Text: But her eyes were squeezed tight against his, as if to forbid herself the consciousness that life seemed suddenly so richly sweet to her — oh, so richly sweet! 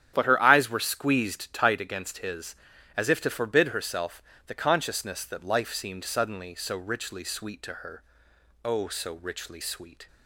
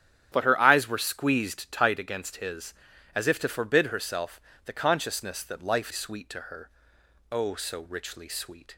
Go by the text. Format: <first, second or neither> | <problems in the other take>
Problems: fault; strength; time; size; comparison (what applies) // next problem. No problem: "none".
first | starts louder than the rest; strong; until 1.3 s; 9.5 dB; strong in the first // pauses between "herself" and "the"; slight; at 4.4 s; 0.24 s long; slight in the first // skips "seemed suddenly so richly"; at 5.9 s